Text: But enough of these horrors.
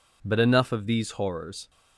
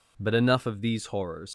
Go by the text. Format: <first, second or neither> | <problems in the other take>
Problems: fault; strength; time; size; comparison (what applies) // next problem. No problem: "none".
first | leaves "horrors" unfinished; at 1.4 s; 105 ms